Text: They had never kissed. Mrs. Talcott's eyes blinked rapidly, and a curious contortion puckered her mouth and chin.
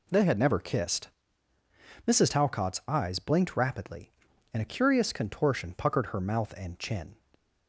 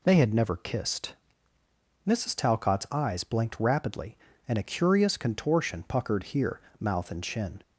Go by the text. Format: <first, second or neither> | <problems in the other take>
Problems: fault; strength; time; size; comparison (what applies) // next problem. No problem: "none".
first | says "here" for "her"; at 6.2 s